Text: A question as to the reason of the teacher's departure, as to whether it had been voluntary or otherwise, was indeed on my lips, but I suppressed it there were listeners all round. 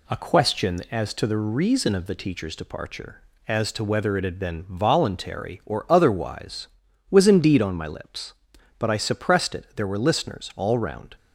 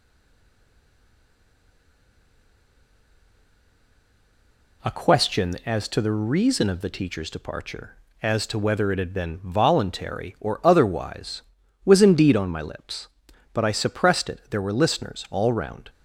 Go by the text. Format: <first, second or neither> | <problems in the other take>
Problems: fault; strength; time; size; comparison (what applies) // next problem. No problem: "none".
first | stays silent before the first word; strong; until 4.8 s; 4.8 s long